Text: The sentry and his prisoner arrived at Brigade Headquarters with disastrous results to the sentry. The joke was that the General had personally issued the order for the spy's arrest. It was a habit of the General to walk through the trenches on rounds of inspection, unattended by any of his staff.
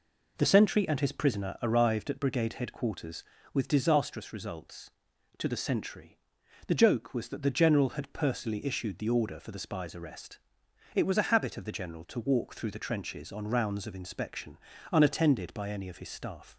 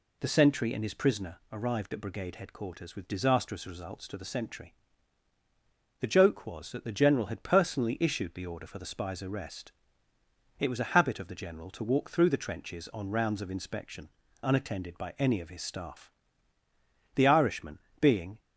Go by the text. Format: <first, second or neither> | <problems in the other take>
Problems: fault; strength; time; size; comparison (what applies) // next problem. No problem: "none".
first | goes on to say "The Irishman being"; noticeable; from 17.1 s on; 1.2 s long